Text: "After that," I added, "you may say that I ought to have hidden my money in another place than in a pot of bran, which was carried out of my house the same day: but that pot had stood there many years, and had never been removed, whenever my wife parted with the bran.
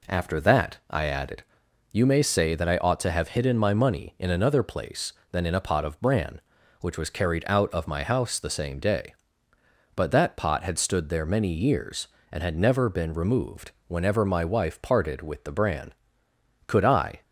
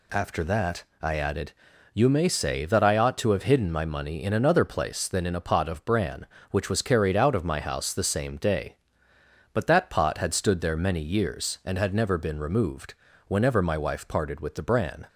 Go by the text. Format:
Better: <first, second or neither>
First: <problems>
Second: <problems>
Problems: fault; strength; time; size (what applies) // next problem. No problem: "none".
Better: second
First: goes on to say "Could I"; from 16.6 s on; 0.54 s long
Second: none